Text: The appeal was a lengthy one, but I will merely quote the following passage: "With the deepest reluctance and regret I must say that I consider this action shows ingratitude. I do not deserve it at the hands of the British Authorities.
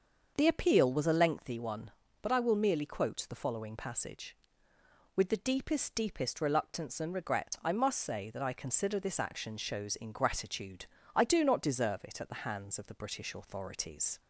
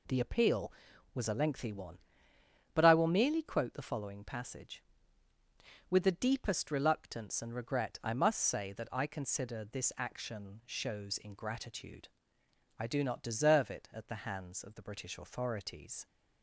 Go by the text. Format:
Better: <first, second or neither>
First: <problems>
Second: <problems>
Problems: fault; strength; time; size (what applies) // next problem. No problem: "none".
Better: second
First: starts louder than the rest; until 1.3 s; 6.5 dB // says "deepest" twice; at 5.9 s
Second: none